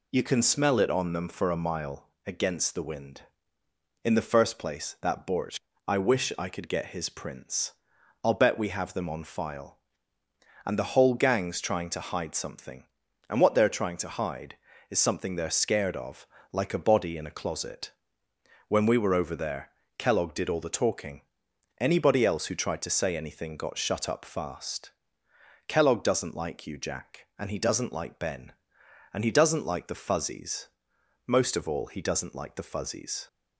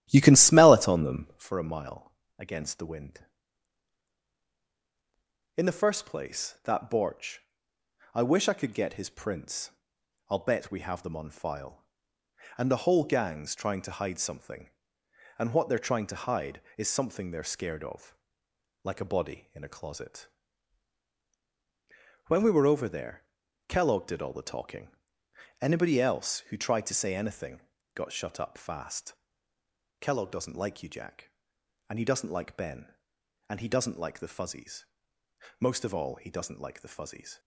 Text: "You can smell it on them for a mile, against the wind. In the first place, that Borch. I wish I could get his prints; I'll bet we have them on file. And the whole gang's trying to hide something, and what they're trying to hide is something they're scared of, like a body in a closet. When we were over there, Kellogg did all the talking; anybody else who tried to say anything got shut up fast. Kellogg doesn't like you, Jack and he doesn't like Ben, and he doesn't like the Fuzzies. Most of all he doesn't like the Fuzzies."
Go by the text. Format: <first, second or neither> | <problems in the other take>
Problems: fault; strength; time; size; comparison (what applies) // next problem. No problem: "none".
first | starts louder than the rest; strong; until 1.5 s; 12.5 dB // pauses between "anything" and "got"; slight; at 27.5 s; 0.34 s long